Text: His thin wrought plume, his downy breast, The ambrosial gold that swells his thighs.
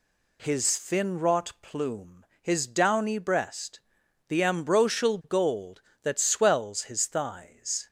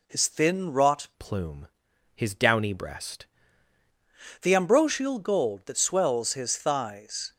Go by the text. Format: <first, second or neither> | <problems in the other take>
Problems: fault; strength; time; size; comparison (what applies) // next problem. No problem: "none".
first | changes voice from "plume" to "breast"; from 1.1 to 3.2 s; 2.1 s long